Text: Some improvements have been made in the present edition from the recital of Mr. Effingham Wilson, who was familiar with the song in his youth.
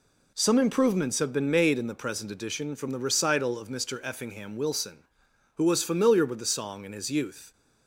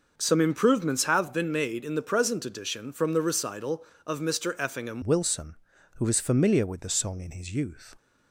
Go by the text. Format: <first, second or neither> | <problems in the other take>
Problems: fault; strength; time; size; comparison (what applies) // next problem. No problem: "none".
first | changes voice at "Wilson"; from 5.0 s on; 2.9 s long